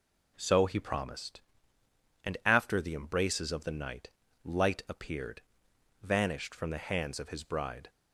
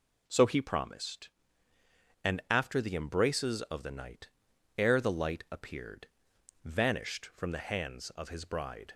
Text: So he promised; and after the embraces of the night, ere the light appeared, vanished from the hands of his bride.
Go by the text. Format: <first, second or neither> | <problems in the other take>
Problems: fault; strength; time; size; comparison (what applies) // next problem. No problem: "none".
second | skips "ere the"; at 4.2 s